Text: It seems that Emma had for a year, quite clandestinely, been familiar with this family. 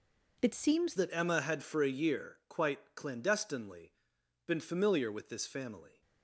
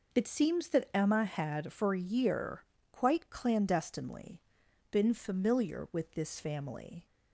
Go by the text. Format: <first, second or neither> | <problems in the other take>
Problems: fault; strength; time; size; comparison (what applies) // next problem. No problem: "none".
second | changes voice at "that"; from 0.9 s on; 5.1 s long